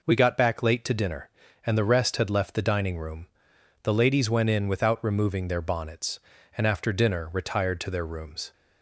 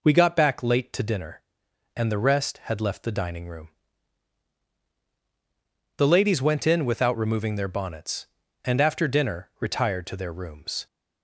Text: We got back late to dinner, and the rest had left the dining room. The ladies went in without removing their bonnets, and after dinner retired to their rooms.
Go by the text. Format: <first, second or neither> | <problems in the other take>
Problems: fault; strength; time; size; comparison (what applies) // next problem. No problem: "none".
neither | none